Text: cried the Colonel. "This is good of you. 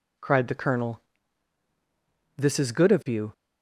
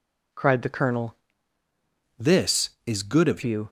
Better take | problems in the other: first | changes voice from "This" to "of"; from 2.1 to 3.4 s; 1.3 s long

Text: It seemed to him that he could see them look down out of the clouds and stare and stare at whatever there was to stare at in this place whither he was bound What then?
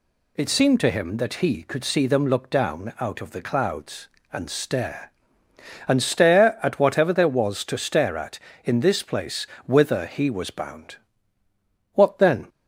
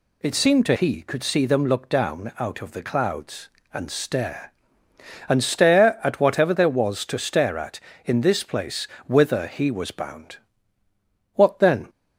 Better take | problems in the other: first | skips "him that"; at 0.7 s // pauses between "place" and "whither"; slight; at 8.8 s; 0.20 s long; slight in the first // pauses between "bound" and "What"; noticeable; at 10.3 s; 0.98 s long; noticeable in the first

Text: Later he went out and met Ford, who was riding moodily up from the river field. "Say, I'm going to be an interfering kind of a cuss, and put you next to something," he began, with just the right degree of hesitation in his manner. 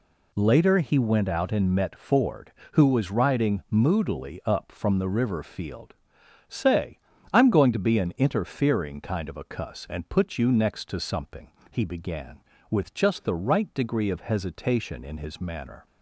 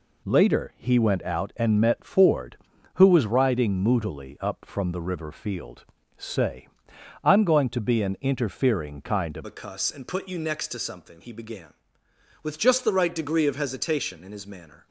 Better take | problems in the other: first | changes voice at "a"; from 9.4 s on; 5.4 s long

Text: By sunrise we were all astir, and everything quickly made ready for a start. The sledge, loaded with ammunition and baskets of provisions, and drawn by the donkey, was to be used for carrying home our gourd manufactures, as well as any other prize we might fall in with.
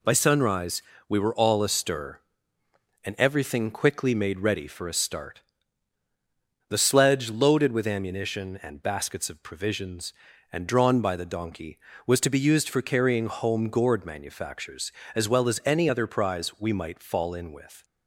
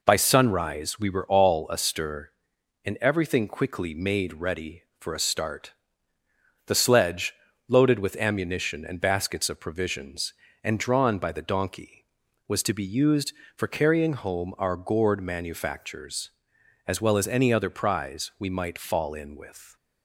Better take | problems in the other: second | pauses between "sunrise" and "we"; slight; at 0.8 s; 0.26 s long // skips "our"; at 13.6 s

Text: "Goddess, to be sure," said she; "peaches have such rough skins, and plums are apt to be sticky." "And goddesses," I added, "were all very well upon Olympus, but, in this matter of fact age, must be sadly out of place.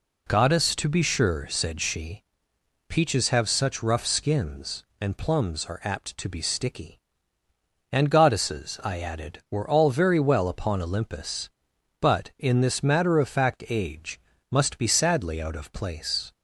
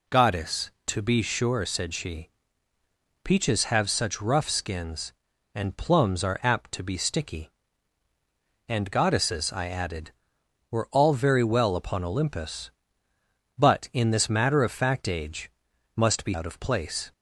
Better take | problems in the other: first | skips "sadly"; at 16.3 s

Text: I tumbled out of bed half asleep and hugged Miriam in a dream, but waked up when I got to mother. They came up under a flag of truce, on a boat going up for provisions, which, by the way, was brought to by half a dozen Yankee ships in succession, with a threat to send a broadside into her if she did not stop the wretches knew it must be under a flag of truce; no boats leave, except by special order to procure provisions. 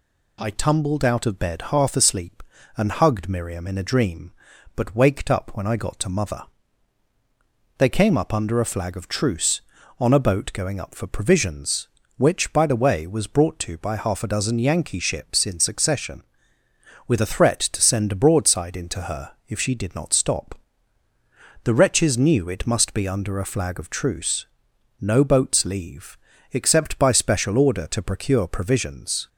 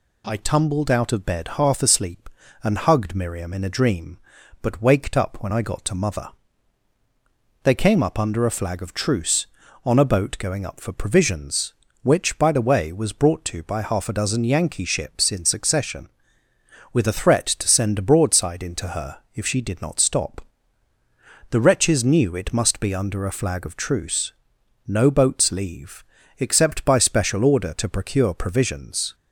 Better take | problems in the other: neither | pauses between "her" and "if"; slight; the same in both // pauses between "stop" and "the"; the same in both

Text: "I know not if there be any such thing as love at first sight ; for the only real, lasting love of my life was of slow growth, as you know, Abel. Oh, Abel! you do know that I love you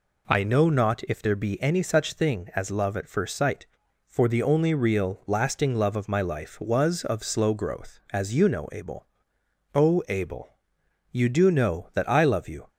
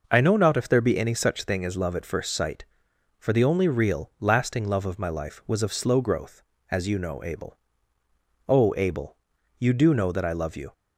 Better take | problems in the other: neither | none

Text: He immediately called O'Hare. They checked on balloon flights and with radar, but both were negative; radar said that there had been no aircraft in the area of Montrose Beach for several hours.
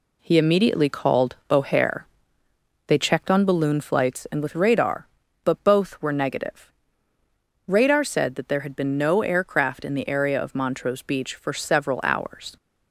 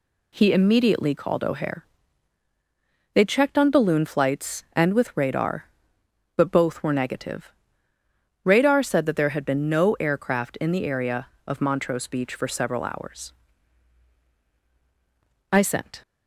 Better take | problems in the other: first | goes on to say "I sent"; from 15.5 s on; 0.50 s long

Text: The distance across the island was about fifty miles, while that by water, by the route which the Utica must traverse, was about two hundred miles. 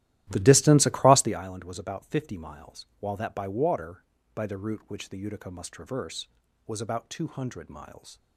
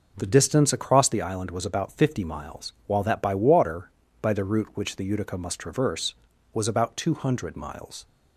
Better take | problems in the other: second | starts louder than the rest; strong; until 1.5 s; 14.5 dB

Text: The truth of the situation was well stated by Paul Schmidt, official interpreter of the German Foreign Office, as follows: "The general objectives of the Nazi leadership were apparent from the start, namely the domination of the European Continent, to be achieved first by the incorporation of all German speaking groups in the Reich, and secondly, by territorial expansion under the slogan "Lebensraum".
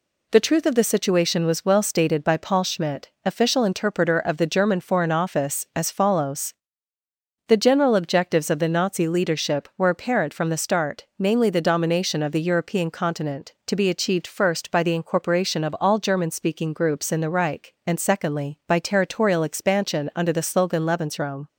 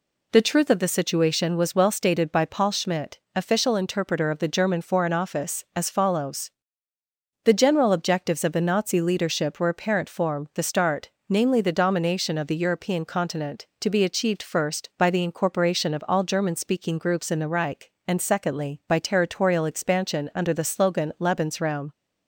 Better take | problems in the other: first | says "form" for "from"; at 10.0 s

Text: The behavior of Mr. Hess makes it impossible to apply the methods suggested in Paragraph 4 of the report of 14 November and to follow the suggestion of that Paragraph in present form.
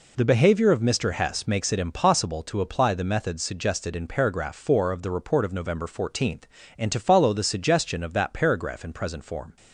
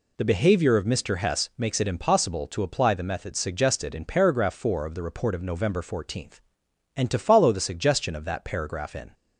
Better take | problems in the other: first | stops before "present form"; at 9.1 s

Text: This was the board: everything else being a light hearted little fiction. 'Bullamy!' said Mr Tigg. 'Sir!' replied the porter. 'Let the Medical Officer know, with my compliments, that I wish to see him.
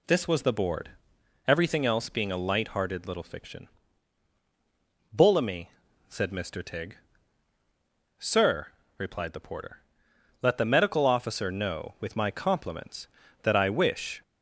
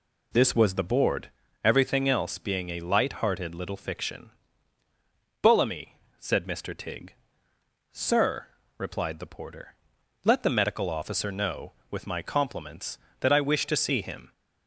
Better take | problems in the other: second | stops before "to see him"; at 14.2 s

